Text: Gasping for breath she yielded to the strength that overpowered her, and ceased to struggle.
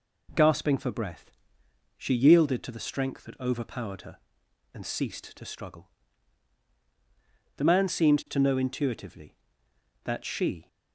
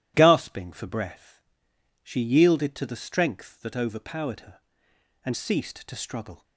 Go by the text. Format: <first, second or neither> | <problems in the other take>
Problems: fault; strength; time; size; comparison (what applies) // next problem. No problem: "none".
second | pauses between "breath" and "she"; noticeable; at 1.3 s; 0.66 s long; noticeable in the second // goes on to say "The man seemed to know intuitively that she"; strong; from 7.5 s on; 3.0 s long